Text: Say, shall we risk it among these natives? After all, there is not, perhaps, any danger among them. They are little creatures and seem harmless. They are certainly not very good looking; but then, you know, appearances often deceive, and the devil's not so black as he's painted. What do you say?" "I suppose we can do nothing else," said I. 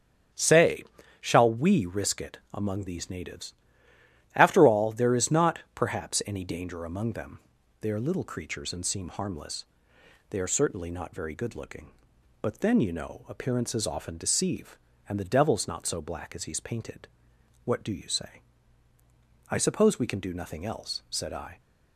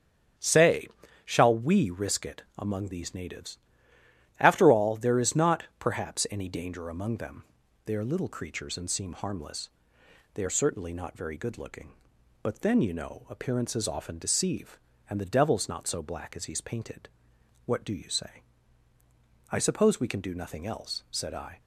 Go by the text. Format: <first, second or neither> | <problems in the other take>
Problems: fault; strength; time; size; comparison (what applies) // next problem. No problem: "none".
neither | starts louder than the rest; strong; the same in both